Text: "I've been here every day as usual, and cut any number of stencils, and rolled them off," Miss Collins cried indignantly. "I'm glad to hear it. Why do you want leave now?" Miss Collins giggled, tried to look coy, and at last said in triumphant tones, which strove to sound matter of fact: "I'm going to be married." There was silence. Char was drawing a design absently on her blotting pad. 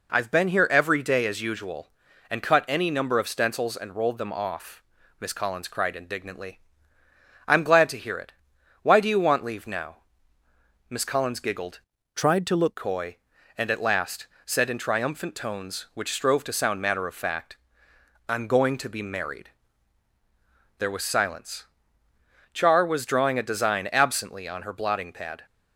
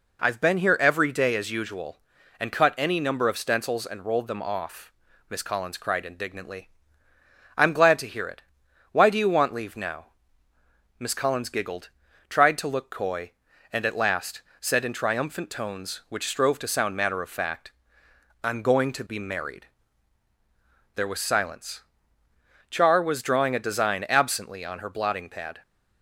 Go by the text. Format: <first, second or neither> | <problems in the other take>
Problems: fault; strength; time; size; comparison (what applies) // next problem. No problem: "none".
second | changes voice from "tried" to "look"; from 12.1 to 12.7 s; 0.6 s long // pauses between "last" and "said"; slight; at 14.2 s; 0.20 s long; slight in the second